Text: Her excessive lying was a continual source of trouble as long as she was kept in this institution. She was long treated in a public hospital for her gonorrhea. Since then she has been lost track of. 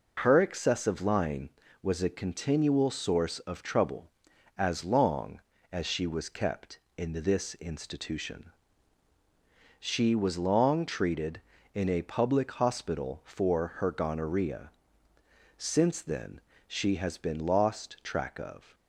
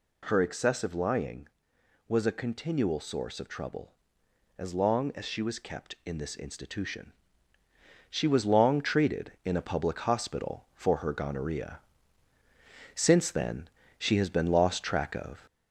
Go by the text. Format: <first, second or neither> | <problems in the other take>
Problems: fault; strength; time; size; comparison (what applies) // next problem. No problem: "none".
first | gets louder; slight; throughout; 2.5 dB // pauses between "then" and "she"; slight; at 13.6 s; 0.32 s long; slight in the first